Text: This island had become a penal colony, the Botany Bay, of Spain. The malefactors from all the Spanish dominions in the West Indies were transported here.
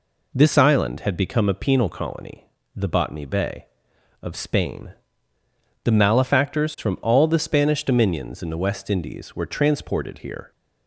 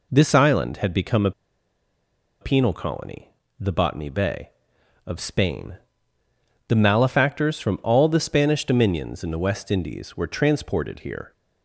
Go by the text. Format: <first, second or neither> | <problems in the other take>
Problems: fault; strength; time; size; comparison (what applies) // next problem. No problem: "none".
first | pauses between "a" and "penal"; at 1.3 s; 1.1 s long